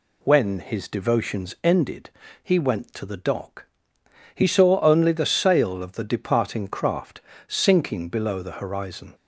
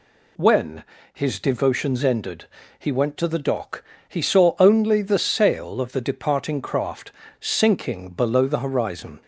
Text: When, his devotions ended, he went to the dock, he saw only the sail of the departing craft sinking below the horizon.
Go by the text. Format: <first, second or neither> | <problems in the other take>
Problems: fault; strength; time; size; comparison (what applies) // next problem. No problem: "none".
neither | pauses between "craft" and "sinking"; slight; the same in both